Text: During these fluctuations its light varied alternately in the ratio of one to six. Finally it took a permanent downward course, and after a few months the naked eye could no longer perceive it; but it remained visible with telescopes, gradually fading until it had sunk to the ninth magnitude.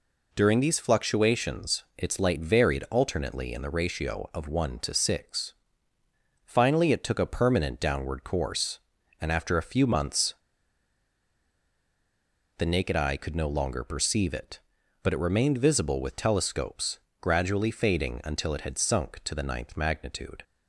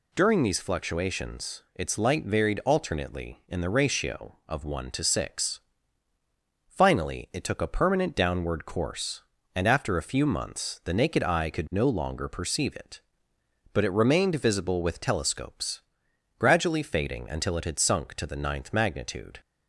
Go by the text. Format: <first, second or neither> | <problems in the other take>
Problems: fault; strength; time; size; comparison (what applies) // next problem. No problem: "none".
second | pauses between "months" and "the"; strong; at 10.3 s; 2.2 s long